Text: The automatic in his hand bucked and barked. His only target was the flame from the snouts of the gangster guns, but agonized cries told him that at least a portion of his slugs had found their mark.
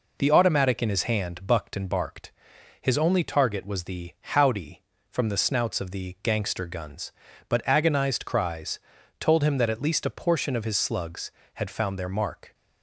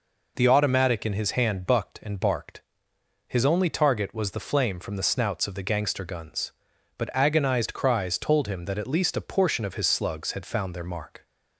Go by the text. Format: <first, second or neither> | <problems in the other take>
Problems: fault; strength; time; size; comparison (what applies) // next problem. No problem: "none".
second | says "howdy" for "flame"; at 4.2 s // pauses between "cries" and "told"; at 8.7 s; 0.40 s long